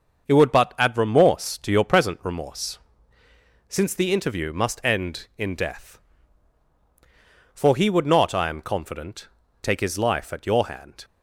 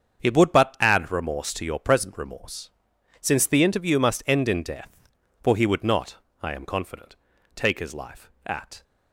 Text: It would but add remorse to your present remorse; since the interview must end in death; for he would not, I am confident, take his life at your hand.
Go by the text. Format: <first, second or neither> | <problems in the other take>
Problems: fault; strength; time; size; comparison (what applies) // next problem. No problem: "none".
first | starts louder than the rest; strong; until 1.2 s; 7.5 dB; also in the first // stops before "your hand"; at 8.8 s